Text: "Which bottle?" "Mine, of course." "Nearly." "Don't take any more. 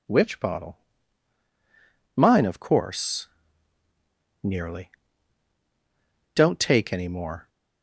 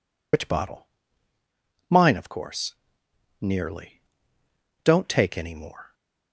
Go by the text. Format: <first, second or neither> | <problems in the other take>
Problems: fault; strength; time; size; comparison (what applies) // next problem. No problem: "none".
first | loses the start of "Which"; at 0.3 s; 55 ms